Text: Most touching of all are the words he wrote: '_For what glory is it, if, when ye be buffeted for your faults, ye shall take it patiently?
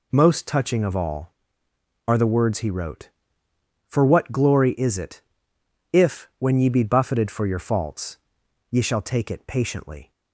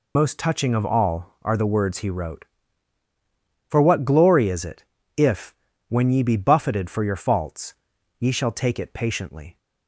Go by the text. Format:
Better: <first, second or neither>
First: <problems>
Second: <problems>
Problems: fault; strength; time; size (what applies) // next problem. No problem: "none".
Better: first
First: none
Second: loses the start of "Most"; at 0.1 s; 35 ms